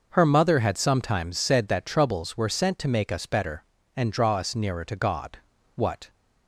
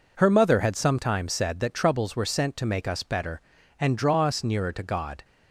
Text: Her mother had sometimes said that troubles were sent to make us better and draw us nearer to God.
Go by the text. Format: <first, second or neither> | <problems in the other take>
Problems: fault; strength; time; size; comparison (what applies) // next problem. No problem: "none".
second | goes on to say "What"; slight; from 5.7 s on; 0.34 s long